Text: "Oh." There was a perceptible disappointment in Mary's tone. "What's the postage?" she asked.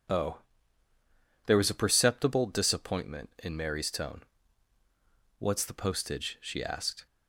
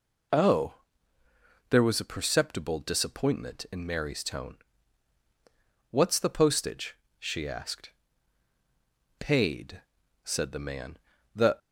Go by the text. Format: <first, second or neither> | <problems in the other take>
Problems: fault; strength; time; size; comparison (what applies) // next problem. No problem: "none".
first | goes on to say "Paid said the man The"; strong; from 9.1 s on; 2.4 s long